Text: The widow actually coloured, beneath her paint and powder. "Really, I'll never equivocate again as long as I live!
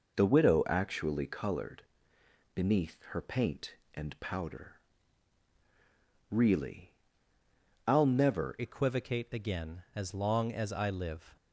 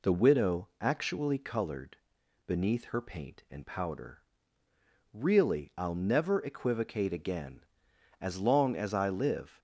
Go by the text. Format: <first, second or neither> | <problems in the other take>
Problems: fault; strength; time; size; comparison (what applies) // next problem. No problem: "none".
second | changes voice at "equivocate"; from 8.5 s on; 2.8 s long